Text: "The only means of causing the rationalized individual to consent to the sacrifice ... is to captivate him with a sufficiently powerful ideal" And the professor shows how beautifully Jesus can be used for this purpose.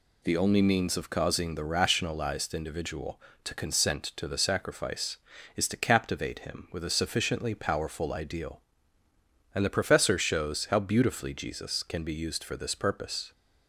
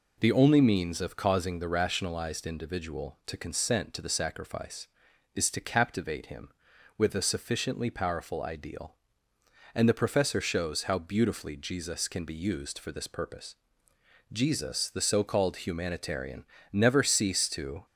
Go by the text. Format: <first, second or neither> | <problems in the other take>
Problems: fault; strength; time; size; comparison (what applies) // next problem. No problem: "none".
first | goes on to say "Jesus the so called humanitarian never ceased to"; strong; from 14.3 s on; 3.5 s long